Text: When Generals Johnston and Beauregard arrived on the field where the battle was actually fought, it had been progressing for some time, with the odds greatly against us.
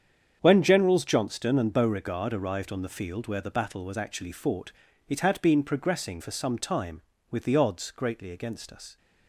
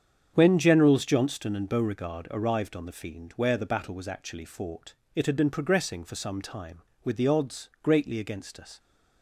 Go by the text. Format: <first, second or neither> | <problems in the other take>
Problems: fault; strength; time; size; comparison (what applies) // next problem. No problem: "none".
first | starts louder than the rest; strong; until 1.3 s; 8 dB; strong in the first // says "fiend" for "field"; at 2.9 s